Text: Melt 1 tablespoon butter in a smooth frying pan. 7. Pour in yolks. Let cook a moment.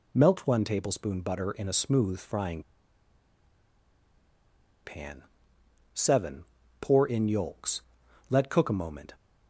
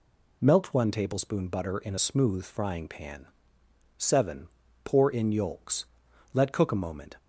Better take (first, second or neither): second